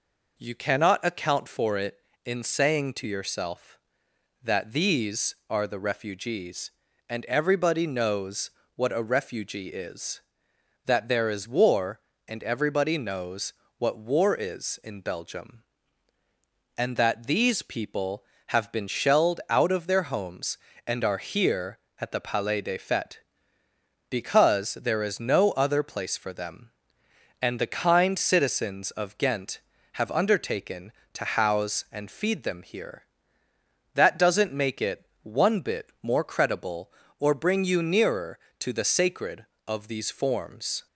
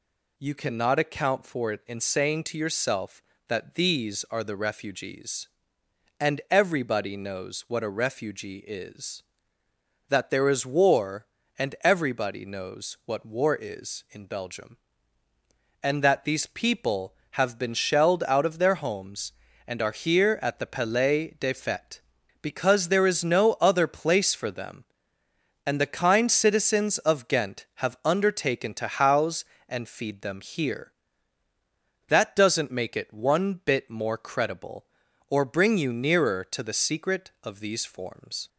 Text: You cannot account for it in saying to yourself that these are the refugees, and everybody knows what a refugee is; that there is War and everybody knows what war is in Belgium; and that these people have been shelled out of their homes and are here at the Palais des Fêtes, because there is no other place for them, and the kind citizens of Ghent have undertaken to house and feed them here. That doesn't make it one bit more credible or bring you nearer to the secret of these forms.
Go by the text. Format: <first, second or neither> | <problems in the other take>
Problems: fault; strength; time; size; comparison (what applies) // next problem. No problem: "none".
second | pauses between "knows" and "what"; slight; at 8.5 s; 0.24 s long // pauses between "knows" and "what"; slight; at 13.5 s; 0.24 s long // pauses between "it" and "one"; slight; at 35.0 s; 0.16 s long // says "sacred" for "secret"; at 38.8 s